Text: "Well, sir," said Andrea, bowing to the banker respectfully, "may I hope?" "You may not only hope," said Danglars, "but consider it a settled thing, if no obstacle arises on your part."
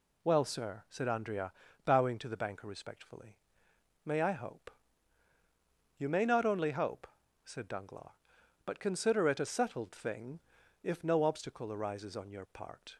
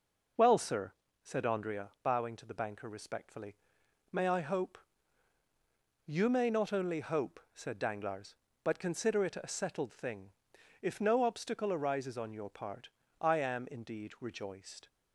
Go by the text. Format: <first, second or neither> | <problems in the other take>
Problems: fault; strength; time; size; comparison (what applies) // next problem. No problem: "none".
first | goes on to say "I am indeed rejoiced"; from 13.2 s on; 1.6 s long